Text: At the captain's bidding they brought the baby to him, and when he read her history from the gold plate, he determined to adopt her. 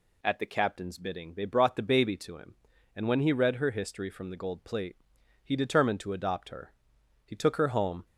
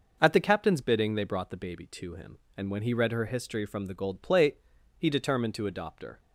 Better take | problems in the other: second | goes on to say "He took her home"; noticeable; from 7.2 s on; 0.80 s long

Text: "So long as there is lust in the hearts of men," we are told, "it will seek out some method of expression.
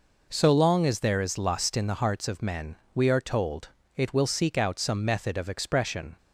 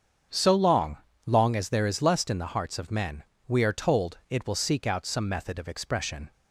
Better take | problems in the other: first | starts louder than the rest; strong; until 1.6 s; 7.5 dB // says "long" twice; at 1.2 s

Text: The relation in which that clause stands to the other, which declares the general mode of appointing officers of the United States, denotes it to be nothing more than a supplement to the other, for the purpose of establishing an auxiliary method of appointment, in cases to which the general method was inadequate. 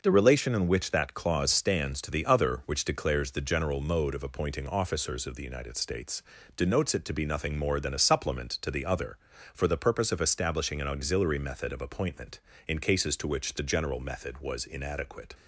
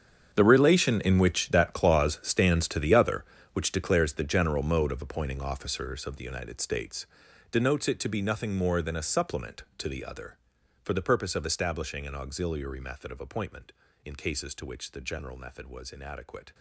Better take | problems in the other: first | gets quieter; strong; throughout; 16 dB

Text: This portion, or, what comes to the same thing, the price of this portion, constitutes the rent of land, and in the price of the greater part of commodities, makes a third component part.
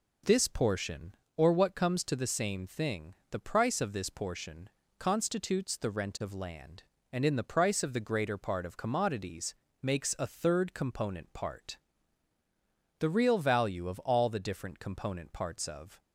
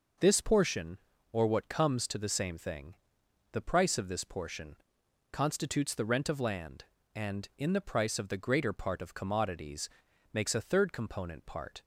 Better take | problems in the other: second | goes on to say "The real value of all the different component parts of"; strong; from 12.9 s on; 3.0 s long

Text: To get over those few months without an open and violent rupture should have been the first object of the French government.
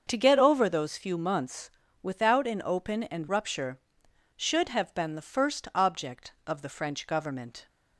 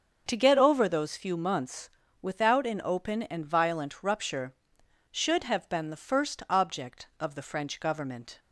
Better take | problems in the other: second | starts louder than the rest; until 1.0 s; 6.5 dB; also in the second // pauses between "months" and "without"; slight; at 1.6 s; 0.32 s long; slight in the second // skips "violent"; at 3.2 s

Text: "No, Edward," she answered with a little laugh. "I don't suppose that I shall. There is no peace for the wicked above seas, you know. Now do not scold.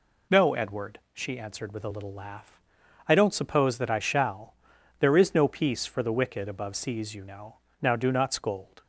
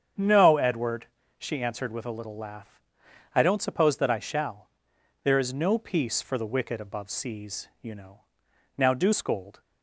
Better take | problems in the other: first | starts louder than the rest; strong; until 1.4 s; 7.5 dB // skips "not"; at 9.1 s

